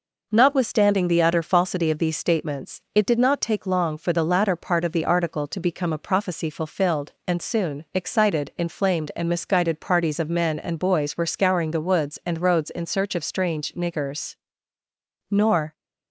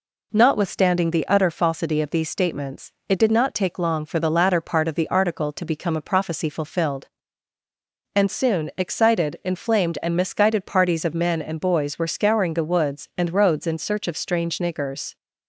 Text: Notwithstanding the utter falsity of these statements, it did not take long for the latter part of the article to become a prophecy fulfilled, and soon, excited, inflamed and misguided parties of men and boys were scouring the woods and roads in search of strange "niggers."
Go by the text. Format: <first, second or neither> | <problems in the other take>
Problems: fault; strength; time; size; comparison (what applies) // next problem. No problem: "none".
second | goes on to say "Nor"; slight; from 15.2 s on; 0.44 s long